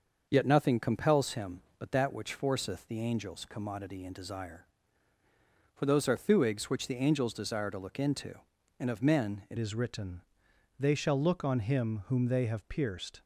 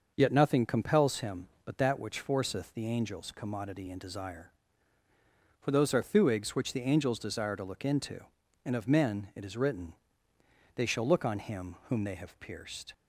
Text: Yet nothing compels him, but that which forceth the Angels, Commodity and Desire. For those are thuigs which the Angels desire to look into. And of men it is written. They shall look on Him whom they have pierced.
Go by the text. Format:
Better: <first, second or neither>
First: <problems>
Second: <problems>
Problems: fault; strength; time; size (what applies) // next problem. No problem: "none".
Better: second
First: starts louder than the rest; until 1.3 s; 6.5 dB // changes voice at "is"; from 9.5 s on; 3.7 s long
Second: starts louder than the rest; noticeable; until 1.1 s; 6 dB